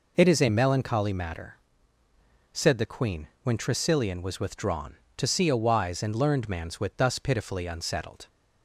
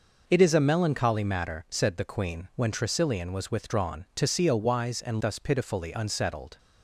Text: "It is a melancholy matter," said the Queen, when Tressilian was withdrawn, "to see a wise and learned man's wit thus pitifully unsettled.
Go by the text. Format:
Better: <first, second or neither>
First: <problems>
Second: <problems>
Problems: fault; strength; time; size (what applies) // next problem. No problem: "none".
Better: first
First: none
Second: skips "learned man's wit"; at 5.2 s